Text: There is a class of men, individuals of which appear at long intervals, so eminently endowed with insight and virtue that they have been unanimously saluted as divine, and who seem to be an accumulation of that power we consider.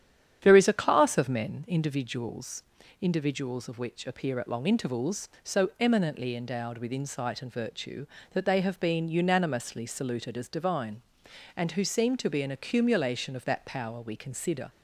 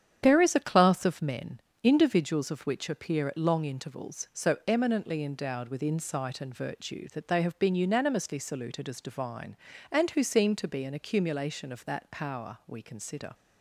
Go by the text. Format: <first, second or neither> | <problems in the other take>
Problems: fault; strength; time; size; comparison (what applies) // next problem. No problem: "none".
second | starts louder than the rest; strong; until 1.4 s; 9.5 dB; strong in the second // says "individuals" twice; at 3.0 s